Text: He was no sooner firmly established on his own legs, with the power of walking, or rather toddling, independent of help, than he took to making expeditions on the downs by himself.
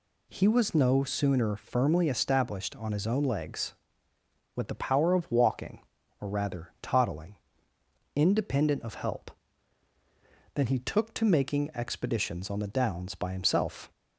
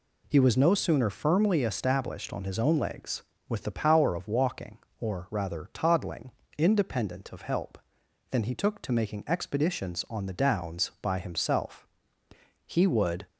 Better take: first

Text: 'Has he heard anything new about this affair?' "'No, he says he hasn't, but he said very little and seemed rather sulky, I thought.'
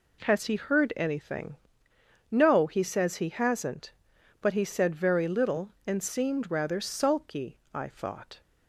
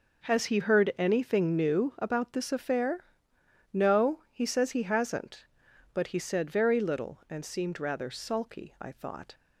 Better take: second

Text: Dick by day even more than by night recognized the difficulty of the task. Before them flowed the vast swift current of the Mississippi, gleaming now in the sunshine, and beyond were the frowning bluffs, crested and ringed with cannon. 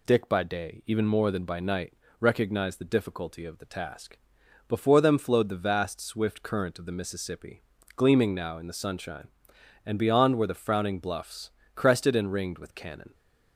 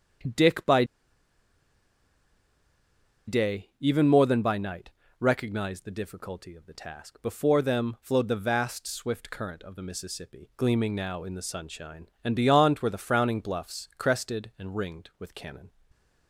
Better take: first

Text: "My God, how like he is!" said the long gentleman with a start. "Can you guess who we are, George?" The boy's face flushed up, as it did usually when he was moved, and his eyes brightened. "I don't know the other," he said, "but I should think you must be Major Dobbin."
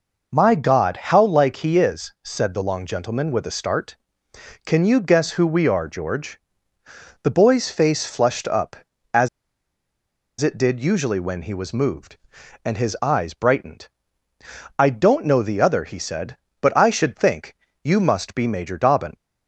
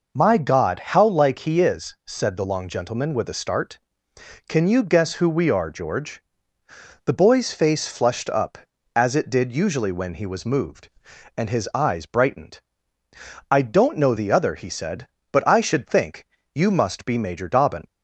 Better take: second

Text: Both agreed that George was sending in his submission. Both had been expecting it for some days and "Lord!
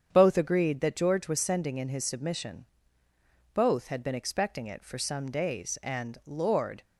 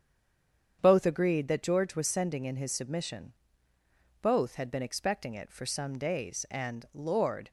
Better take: first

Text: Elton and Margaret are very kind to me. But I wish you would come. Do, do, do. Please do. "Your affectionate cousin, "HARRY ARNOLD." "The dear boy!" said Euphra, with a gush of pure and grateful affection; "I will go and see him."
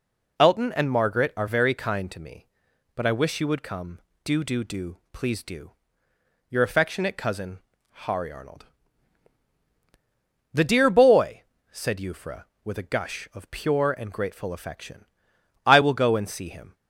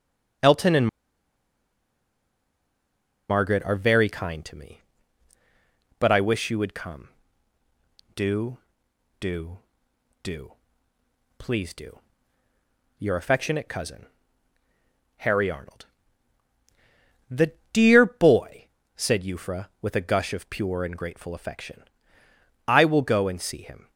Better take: first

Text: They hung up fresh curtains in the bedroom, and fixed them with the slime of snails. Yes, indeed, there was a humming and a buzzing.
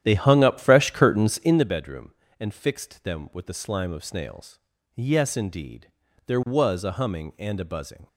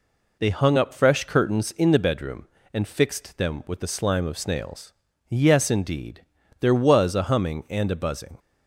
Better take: second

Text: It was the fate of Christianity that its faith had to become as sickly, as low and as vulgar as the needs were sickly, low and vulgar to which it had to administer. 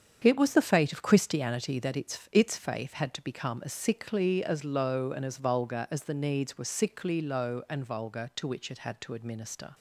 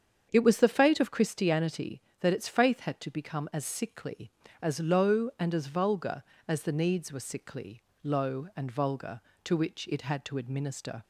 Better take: second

